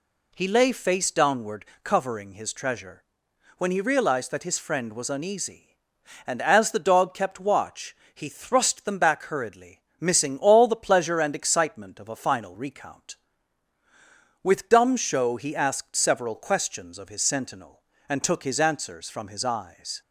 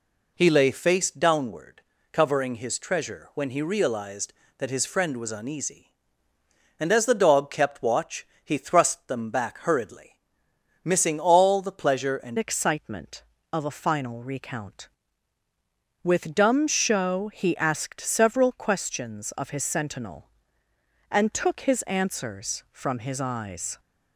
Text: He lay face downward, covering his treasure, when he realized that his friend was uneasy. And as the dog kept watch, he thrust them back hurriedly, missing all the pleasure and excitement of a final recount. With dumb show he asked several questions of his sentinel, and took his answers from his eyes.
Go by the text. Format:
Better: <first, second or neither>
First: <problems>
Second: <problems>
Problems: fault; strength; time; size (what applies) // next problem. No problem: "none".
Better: first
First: none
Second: changes voice at "excitement"; from 12.3 s on; 11.4 s long